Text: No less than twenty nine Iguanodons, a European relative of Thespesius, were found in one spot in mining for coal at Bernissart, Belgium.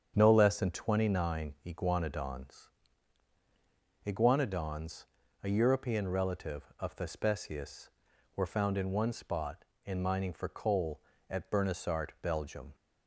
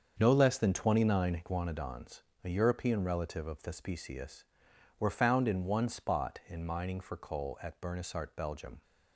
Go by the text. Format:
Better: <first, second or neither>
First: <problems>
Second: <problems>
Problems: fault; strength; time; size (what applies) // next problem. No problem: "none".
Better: second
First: starts louder than the rest; strong; until 1.1 s; 7.5 dB // says "Iguanodons" twice; at 4.0 s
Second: starts louder than the rest; until 1.2 s; 6.5 dB